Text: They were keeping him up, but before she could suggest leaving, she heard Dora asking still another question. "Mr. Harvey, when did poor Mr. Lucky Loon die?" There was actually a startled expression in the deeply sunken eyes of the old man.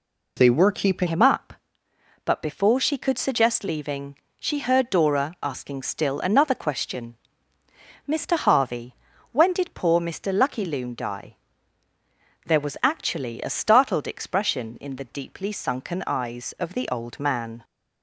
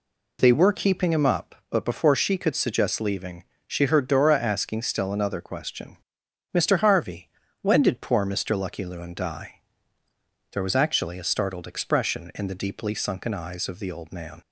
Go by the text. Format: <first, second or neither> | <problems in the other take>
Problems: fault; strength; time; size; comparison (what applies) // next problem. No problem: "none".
second | changes voice at "him"; from 1.0 s on; 16.6 s long